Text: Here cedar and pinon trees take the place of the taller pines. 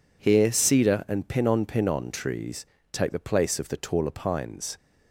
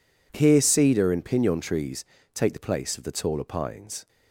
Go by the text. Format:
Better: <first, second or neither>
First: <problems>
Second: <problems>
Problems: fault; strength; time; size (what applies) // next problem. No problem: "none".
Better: second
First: says "pinon" twice; at 1.6 s // pauses between "trees" and "take"; slight; at 2.6 s; 0.26 s long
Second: pauses between "trees" and "take"; slight; at 2.0 s; 0.30 s long